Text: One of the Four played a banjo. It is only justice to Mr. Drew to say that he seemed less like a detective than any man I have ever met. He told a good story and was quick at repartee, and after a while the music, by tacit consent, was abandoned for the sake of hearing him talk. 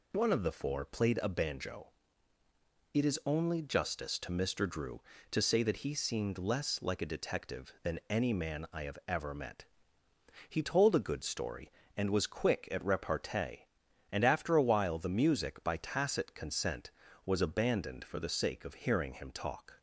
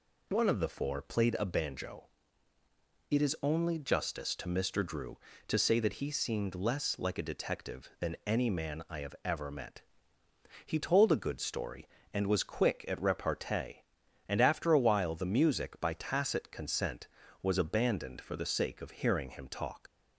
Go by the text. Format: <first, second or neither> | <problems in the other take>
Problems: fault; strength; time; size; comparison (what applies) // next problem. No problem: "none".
first | leaves "talk" unfinished; at 19.8 s; 90 ms